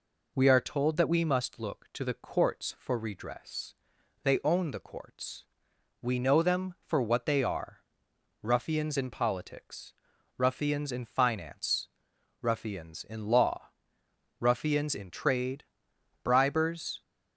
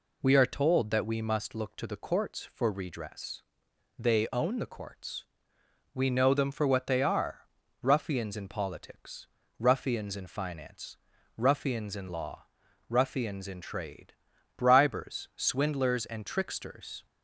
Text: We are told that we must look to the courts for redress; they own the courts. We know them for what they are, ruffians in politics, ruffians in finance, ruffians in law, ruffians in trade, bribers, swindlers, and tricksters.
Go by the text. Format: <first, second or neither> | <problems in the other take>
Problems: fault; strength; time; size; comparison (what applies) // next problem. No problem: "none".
second | stops before "swindlers and tricksters"; at 17.0 s